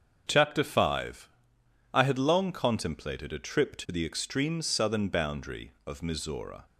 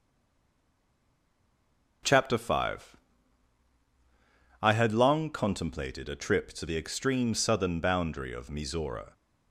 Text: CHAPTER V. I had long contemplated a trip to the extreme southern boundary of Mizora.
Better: first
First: starts louder than the rest; until 1.2 s; 6.5 dB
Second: stays silent before the first word; noticeable; until 2.0 s; 2.0 s long // starts louder than the rest; noticeable; until 4.6 s; 6 dB

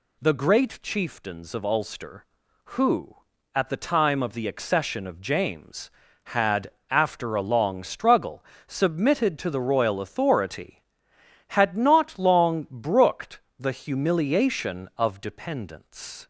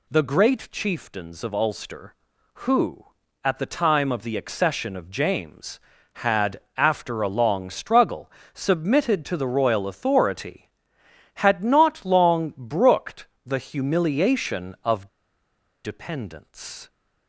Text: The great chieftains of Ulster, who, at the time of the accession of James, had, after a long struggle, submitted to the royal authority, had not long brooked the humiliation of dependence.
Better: first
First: pauses between "brooked" and "the"; slight; at 13.4 s; 0.18 s long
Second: pauses between "brooked" and "the"; slight; at 13.2 s; 0.18 s long // pauses between "of" and "dependence"; noticeable; at 15.0 s; 0.76 s long

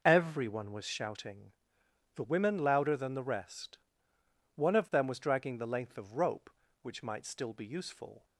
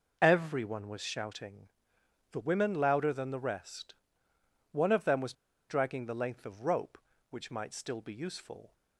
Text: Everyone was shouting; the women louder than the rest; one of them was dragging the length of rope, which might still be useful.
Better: first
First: none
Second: pauses between "was" and "dragging"; at 5.3 s; 0.36 s long

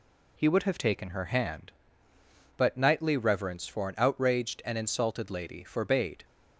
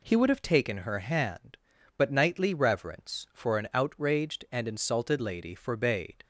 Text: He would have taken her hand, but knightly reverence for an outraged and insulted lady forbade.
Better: neither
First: none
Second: none

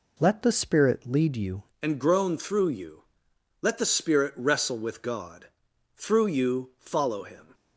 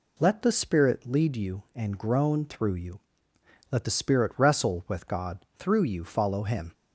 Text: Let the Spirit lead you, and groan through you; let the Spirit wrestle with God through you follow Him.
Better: second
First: changes voice at "and"; from 1.8 s on; 5.7 s long // pauses between "God" and "through"; noticeable; at 5.4 s; 0.48 s long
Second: none

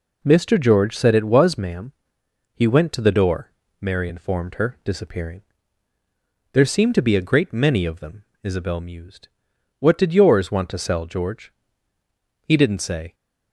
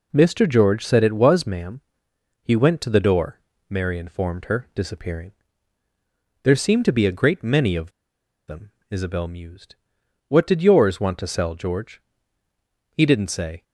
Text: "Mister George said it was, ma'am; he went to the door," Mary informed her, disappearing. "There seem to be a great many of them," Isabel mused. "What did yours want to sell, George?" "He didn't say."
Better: first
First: none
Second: pauses between "of" and "them"; noticeable; at 7.9 s; 0.57 s long

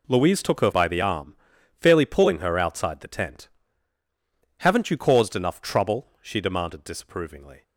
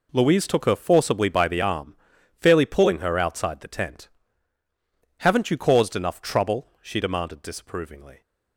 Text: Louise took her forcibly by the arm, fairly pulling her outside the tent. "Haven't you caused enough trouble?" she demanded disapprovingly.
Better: second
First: skips "forcibly"; at 0.7 s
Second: none

